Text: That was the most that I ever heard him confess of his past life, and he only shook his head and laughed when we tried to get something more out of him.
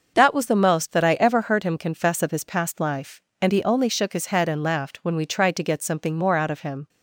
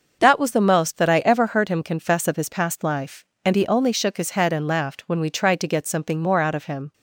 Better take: neither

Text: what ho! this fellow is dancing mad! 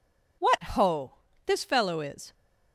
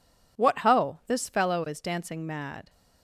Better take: second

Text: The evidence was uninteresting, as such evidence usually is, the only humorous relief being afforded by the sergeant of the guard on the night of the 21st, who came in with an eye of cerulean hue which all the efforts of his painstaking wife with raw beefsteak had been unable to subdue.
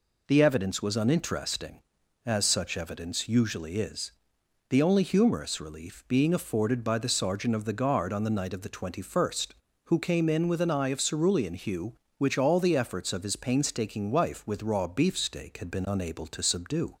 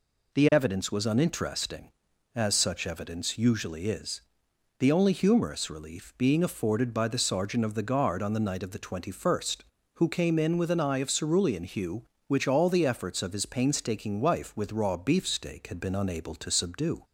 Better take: neither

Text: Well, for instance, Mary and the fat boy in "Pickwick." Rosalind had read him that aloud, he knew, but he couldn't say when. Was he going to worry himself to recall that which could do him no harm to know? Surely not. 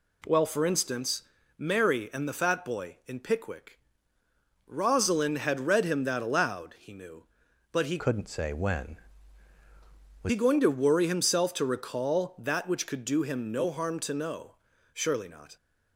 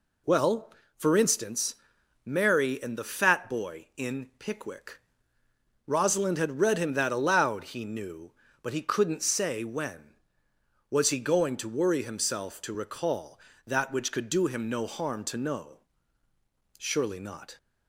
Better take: second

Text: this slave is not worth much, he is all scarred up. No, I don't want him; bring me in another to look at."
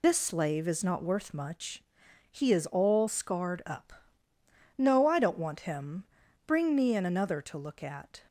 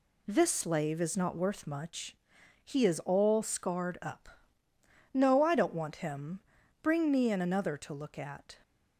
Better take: second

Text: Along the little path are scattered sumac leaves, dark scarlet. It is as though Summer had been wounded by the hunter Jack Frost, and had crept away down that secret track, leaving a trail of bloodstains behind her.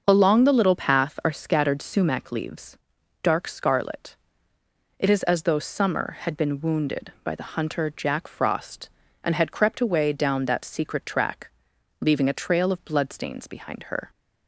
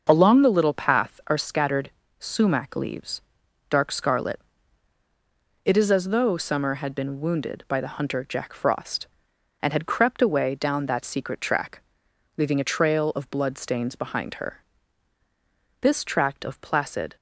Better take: first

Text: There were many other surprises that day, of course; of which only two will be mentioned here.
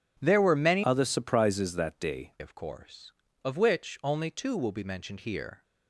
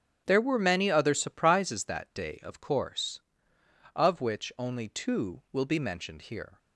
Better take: second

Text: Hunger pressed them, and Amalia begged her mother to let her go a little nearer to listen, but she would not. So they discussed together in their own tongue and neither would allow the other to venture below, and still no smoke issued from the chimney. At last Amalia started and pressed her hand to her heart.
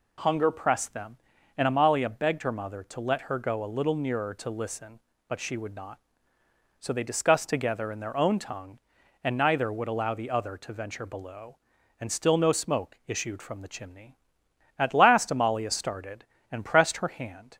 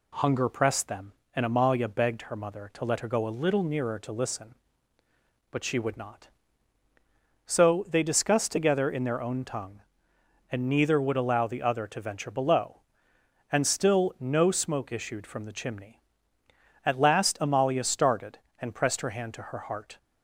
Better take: second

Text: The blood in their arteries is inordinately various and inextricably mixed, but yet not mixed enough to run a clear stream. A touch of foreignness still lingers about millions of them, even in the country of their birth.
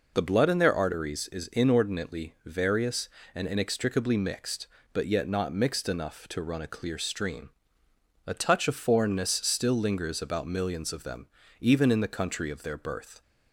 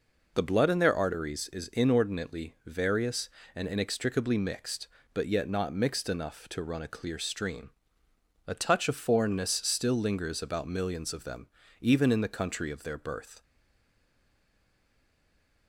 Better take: first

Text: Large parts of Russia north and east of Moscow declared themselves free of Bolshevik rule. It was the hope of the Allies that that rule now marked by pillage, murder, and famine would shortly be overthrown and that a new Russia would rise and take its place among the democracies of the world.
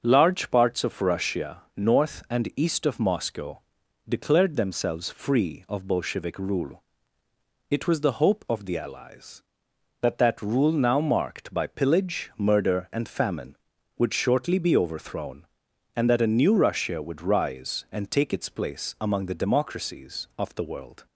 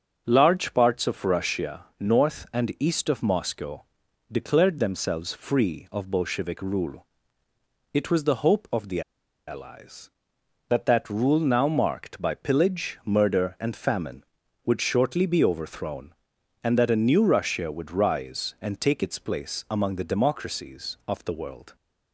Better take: first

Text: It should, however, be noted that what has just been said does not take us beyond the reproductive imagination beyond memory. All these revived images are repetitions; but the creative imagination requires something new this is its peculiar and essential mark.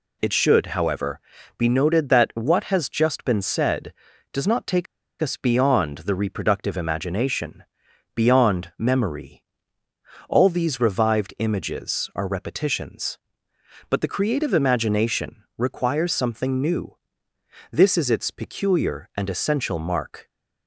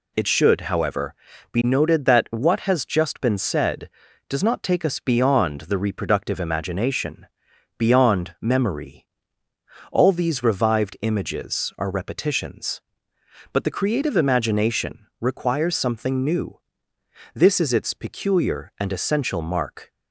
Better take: second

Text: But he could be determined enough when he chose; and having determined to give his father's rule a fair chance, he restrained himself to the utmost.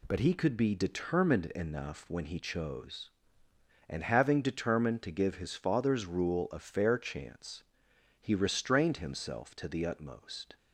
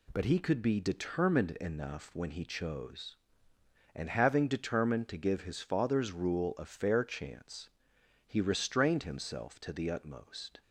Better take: neither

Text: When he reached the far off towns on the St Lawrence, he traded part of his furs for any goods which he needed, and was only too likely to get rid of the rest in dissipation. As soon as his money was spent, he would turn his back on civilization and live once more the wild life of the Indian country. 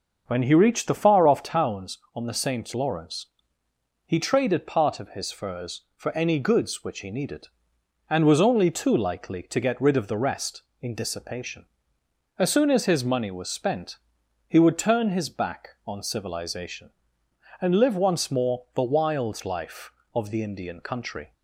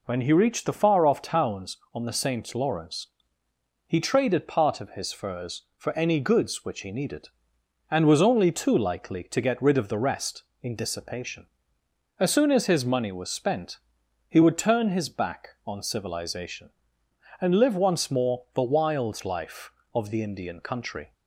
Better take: second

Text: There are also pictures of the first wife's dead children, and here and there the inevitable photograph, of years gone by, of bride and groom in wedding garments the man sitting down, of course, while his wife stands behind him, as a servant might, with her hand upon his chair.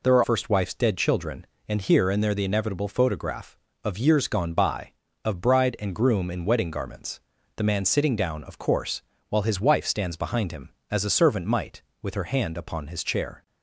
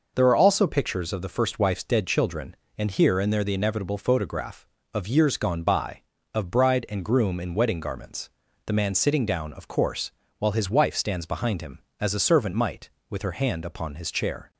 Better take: second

